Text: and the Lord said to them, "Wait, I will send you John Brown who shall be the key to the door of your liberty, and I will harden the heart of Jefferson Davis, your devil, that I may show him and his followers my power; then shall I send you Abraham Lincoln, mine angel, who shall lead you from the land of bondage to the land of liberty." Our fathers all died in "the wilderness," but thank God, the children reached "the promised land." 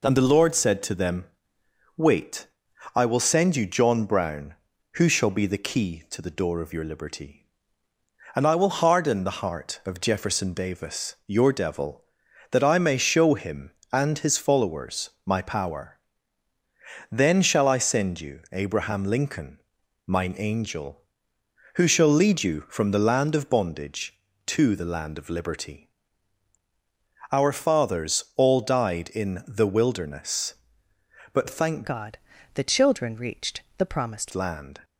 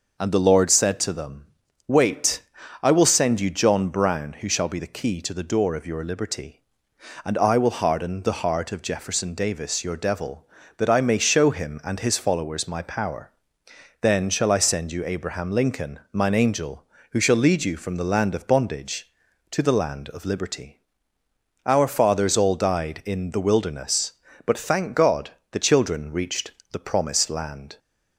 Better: second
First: pauses between "followers" and "my"; slight; at 15.0 s; 0.16 s long // changes voice from "God" to "promised"; from 31.8 to 34.3 s; 2.5 s long // pauses between "reached" and "the"; slight; at 33.6 s; 0.16 s long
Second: pauses between "reached" and "the"; slight; at 26.5 s; 0.18 s long

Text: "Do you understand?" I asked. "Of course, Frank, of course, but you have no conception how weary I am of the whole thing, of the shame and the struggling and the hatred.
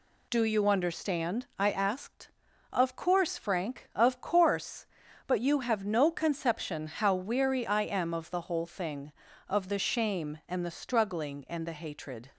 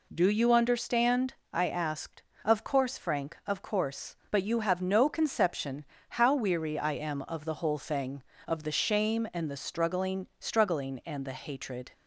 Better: first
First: none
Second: pauses between "conception" and "how"; slight; at 5.8 s; 0.26 s long // says "struggling" twice; at 10.3 s

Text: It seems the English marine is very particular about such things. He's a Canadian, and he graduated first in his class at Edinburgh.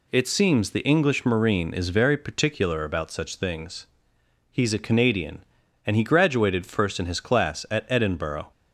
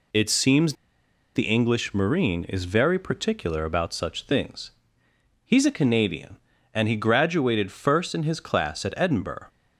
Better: first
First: none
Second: pauses between "seems" and "the"; noticeable; at 0.7 s; 0.60 s long

